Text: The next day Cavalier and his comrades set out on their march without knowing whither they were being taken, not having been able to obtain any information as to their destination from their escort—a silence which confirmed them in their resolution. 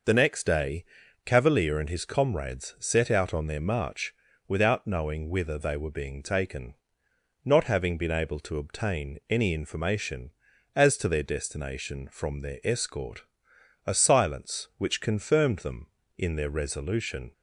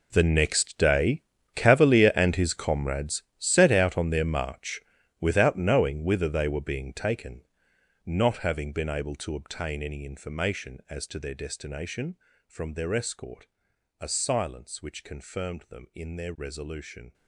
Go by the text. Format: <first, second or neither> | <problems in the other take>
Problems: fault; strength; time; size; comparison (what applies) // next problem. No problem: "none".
first | gets quieter; strong; throughout; 15 dB // pauses between "day" and "Cavalier"; slight; at 1.2 s; 0.32 s long; also in the first // pauses between "comrades" and "set"; slight; at 3.2 s; 0.16 s long // pauses between "march" and "without"; at 4.8 s; 0.40 s long; slight in the first